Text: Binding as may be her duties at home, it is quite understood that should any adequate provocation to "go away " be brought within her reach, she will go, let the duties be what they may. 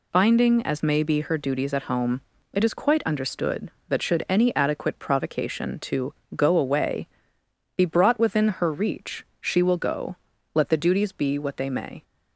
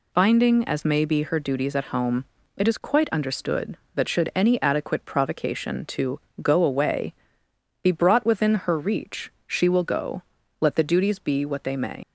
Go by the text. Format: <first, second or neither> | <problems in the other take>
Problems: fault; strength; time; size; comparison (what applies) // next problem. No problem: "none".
first | pauses between "to" and "go"; slight; at 6.1 s; 0.22 s long; slight in the first // leaves "may" unfinished; at 12.0 s; 70 ms